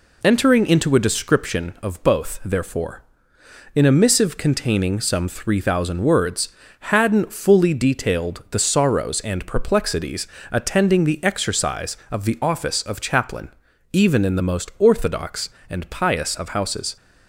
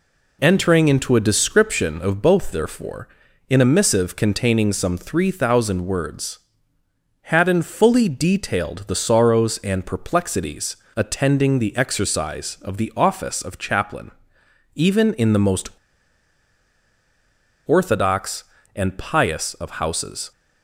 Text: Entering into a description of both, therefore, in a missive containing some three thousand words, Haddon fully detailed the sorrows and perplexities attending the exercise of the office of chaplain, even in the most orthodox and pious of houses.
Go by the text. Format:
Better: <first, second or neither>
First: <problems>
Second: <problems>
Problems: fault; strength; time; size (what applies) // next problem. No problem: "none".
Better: first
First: pauses between "perplexities" and "attending"; slight; at 10.2 s; 0.24 s long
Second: pauses between "perplexities" and "attending"; slight; at 10.7 s; 0.20 s long // pauses between "most" and "orthodox"; strong; at 15.6 s; 1.9 s long